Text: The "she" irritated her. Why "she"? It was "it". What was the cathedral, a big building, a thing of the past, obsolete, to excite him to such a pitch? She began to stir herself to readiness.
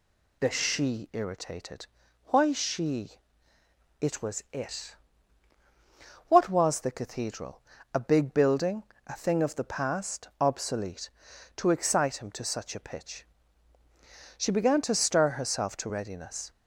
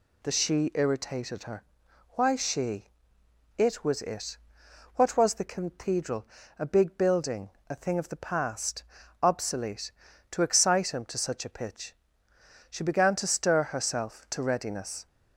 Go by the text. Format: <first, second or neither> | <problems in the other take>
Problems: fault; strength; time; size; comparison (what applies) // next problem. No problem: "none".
second | skips "her"; at 2.0 s